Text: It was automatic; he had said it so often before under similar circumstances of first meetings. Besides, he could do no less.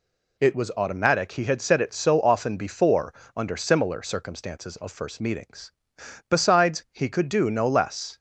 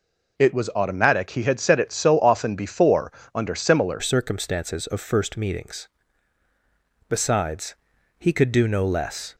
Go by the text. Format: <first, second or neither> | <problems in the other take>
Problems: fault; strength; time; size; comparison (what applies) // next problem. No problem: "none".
first | pauses between "before" and "under"; slight; at 3.0 s; 0.24 s long; slight in the first // changes voice at "circumstances"; from 4.0 s on; 5.3 s long